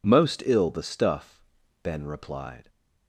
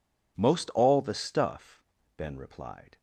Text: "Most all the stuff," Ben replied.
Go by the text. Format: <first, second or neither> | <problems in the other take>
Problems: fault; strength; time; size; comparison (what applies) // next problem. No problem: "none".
second | says "ill" for "all"; at 0.4 s